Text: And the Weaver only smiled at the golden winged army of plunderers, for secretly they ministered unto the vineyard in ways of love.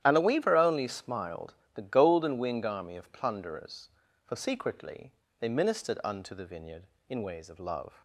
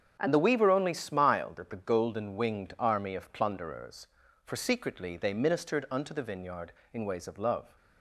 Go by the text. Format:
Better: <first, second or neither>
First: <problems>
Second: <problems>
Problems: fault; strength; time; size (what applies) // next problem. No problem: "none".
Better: second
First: starts louder than the rest; strong; until 1.0 s; 11.5 dB // skips "at"; at 1.6 s // pauses between "secretly" and "they"; slight; at 5.1 s; 0.26 s long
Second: starts louder than the rest; strong; until 1.2 s; 7.5 dB